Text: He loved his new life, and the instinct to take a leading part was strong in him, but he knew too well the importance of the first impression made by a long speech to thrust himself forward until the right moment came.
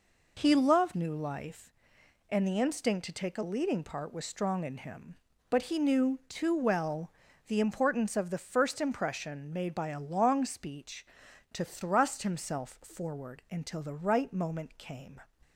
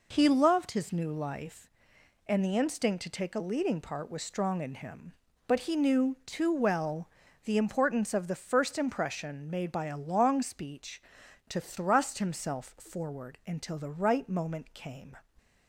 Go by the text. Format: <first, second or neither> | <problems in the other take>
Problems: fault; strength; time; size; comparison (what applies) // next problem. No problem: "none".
second | skips "his"; at 0.9 s // pauses between "well" and "the"; at 7.0 s; 0.38 s long; also in the second